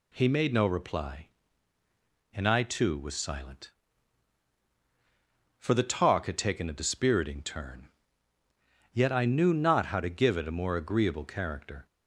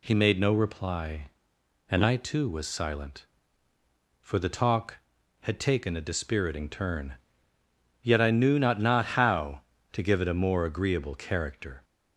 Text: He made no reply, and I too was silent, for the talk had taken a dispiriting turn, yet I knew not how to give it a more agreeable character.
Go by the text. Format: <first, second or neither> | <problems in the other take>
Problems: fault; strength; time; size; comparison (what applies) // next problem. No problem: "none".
first | says "not" twice; at 8.8 s